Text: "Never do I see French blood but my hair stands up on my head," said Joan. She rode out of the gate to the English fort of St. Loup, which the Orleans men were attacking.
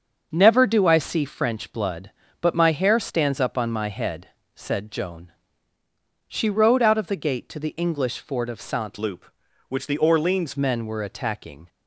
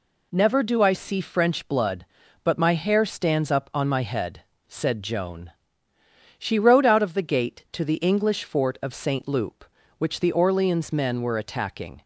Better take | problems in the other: second | starts louder than the rest; until 1.3 s; 6.5 dB // changes voice from "Loup" to "Orleans"; from 8.9 to 10.5 s; 1.6 s long

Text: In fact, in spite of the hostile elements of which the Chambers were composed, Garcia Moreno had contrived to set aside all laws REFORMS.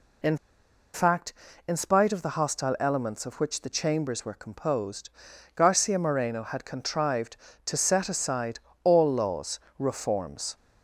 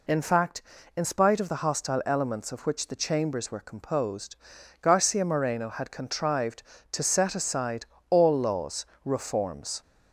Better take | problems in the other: second | pauses between "In" and "fact"; noticeable; at 0.3 s; 0.58 s long // pauses between "aside" and "all"; slight; at 8.5 s; 0.24 s long; slight in the second // pauses between "laws" and "REFORMS"; slight; at 9.5 s; 0.18 s long; slight in the second

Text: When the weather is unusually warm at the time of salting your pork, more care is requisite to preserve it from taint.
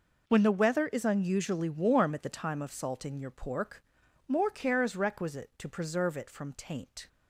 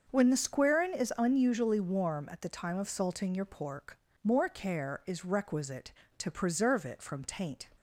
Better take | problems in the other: first | starts louder than the rest; until 1.1 s; 6.5 dB // says "squarin" for "weather"; at 0.3 s

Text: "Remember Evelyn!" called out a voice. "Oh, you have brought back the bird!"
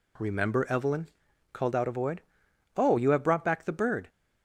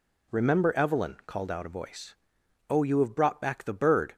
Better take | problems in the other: second | says "void" for "voice"; at 1.9 s

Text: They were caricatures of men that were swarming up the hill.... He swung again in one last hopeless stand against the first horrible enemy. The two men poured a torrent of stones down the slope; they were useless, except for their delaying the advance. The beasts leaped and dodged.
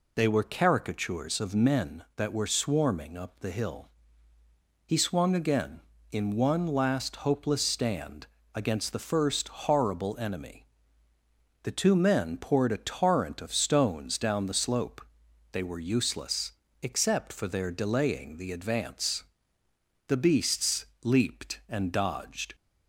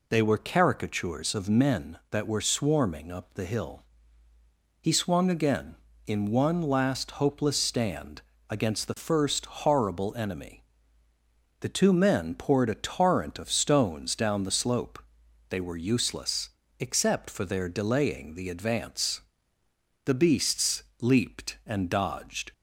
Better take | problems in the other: neither | pauses between "stand" and "against"; slight; the same in both // pauses between "beasts" and "leaped"; slight; the same in both

